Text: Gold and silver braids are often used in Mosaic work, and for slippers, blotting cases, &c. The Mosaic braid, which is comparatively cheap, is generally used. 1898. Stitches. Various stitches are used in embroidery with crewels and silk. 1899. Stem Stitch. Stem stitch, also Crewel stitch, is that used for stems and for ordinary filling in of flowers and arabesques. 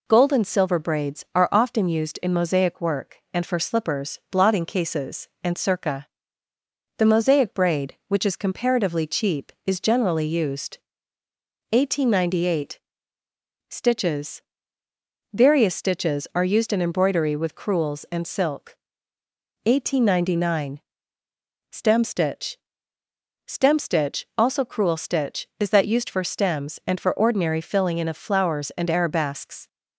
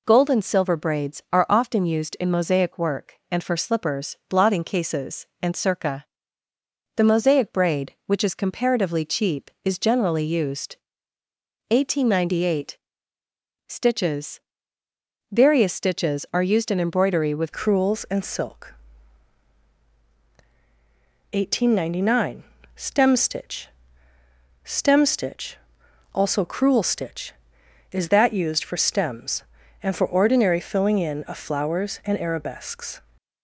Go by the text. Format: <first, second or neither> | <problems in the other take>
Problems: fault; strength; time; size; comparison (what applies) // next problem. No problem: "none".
first | changes voice at "crewels"; from 17.5 s on; 15.5 s long